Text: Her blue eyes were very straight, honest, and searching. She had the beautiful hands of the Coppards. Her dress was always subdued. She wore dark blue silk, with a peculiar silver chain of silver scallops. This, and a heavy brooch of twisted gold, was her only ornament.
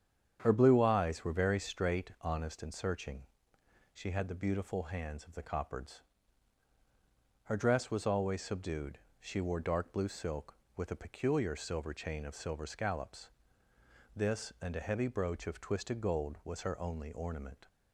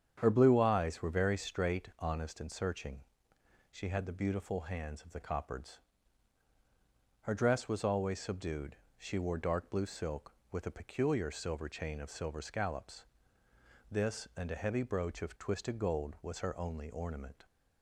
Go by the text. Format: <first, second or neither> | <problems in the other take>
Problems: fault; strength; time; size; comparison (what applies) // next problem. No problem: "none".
neither | starts louder than the rest; strong; the same in both